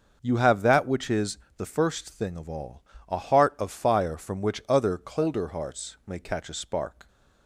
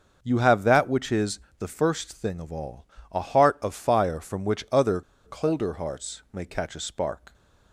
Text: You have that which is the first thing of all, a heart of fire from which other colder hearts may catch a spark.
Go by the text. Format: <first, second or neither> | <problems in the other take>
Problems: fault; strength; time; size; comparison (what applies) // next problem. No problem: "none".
first | starts louder than the rest; noticeable; until 1.2 s; 6 dB; also in the first // pauses between "is" and "the"; slight; at 1.3 s; 0.18 s long; slight in the first // pauses between "other" and "colder"; slight; at 5.0 s; 0.25 s long